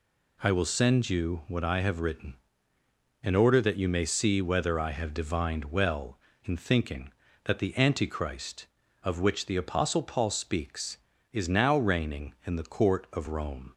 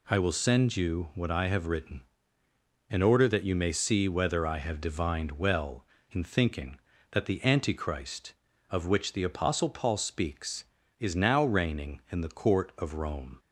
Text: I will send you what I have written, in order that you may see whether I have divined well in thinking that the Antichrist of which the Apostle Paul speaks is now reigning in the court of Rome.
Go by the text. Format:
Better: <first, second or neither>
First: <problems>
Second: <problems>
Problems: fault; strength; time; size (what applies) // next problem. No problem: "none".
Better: neither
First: none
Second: none